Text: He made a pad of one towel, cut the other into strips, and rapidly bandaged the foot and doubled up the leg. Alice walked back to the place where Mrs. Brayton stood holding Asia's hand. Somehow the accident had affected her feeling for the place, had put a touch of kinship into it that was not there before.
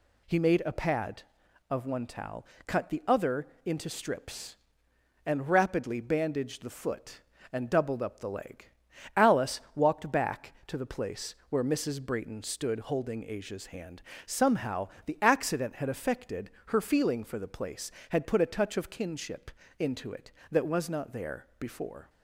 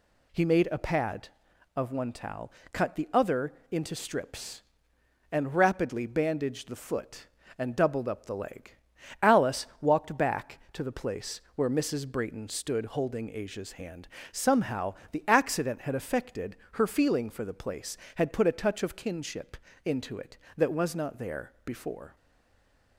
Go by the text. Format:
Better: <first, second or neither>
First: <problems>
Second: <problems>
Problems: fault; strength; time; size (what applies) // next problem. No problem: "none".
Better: first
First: pauses between "other" and "into"; slight; at 3.4 s; 0.18 s long // pauses between "place" and "where"; slight; at 11.3 s; 0.16 s long // pauses between "Somehow" and "the"; slight; at 14.8 s; 0.20 s long // pauses between "affected" and "her"; slight; at 16.5 s; 0.16 s long // pauses between "kinship" and "into"; slight; at 19.4 s; 0.30 s long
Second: pauses between "other" and "into"; slight; at 3.5 s; 0.18 s long // pauses between "place" and "where"; slight; at 11.3 s; 0.16 s long // pauses between "Somehow" and "the"; slight; at 14.9 s; 0.20 s long // pauses between "affected" and "her"; slight; at 16.5 s; 0.16 s long // pauses between "kinship" and "into"; slight; at 19.5 s; 0.30 s long // stays silent after the last word; slight; from 22.1 s on; 0.8 s long